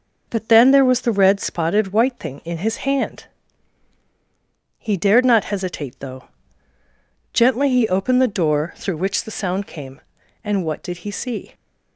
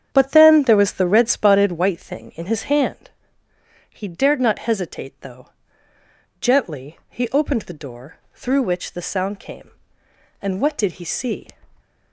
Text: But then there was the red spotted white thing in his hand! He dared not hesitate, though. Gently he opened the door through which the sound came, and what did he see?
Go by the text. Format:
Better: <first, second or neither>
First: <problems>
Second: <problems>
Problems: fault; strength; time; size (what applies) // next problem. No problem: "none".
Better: first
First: none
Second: starts louder than the rest; strong; until 2.0 s; 8.5 dB // pauses between "door" and "through"; slight; at 8.1 s; 0.16 s long